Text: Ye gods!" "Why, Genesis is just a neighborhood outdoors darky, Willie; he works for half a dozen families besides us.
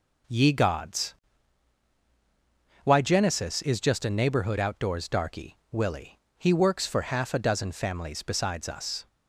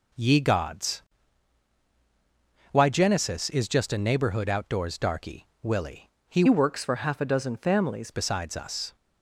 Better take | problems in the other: first | changes voice from "works" to "families"; from 6.4 to 8.1 s; 1.7 s long

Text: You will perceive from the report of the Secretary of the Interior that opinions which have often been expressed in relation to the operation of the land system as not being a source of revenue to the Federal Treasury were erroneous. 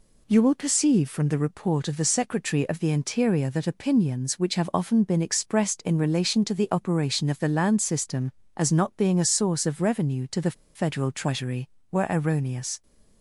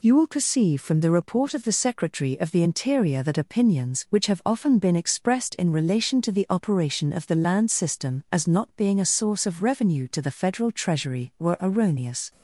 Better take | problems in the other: second | pauses between "the" and "Federal"; slight; at 10.5 s; 0.21 s long

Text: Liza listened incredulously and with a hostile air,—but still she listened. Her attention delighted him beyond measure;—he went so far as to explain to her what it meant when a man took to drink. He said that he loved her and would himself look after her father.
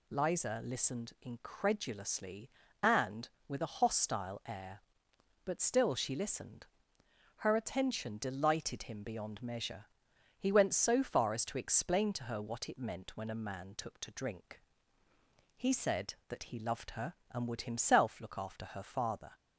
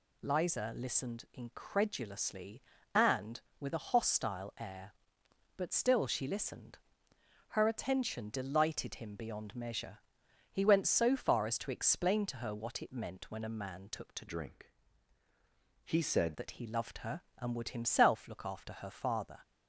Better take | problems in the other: first | changes voice from "drink" to "said"; from 14.2 to 16.3 s; 2.1 s long

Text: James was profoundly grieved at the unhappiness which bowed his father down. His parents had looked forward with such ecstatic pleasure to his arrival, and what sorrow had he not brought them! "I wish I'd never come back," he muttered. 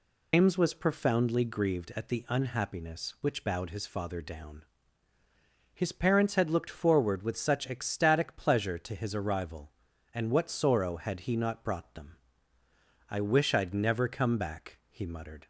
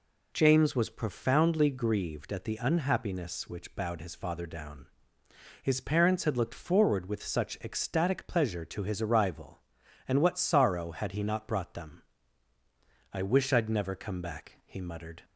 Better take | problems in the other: second | loses the start of "James"; at 0.3 s; 145 ms

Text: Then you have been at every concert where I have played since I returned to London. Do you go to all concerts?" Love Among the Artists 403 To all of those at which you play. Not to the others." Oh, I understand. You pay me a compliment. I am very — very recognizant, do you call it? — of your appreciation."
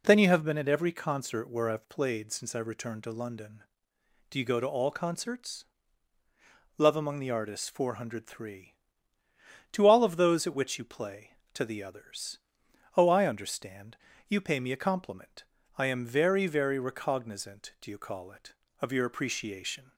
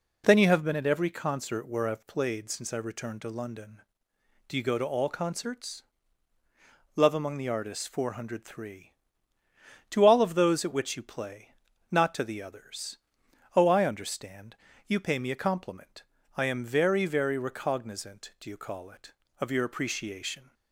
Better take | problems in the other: second | skips "Not"; at 11.4 s

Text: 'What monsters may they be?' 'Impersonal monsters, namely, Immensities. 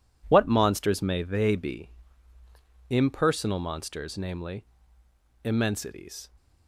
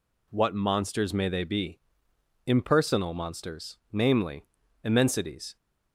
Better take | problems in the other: neither | none

